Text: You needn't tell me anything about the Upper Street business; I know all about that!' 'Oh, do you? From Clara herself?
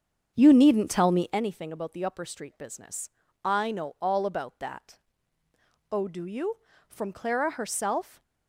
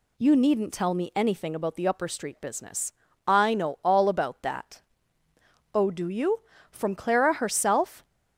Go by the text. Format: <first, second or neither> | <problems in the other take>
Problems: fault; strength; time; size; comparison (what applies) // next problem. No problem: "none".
second | starts louder than the rest; strong; until 1.4 s; 7.5 dB